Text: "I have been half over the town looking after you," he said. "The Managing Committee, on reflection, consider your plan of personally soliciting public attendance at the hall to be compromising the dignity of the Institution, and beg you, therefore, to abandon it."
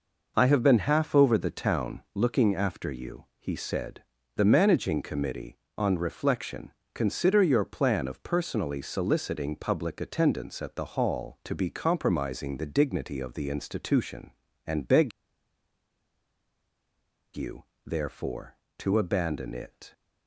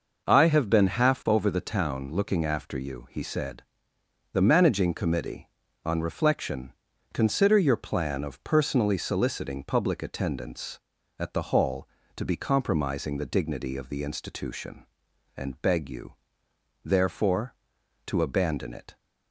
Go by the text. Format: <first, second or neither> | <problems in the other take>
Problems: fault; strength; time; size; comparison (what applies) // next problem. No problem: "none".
second | pauses between "beg" and "you"; strong; at 15.1 s; 2.2 s long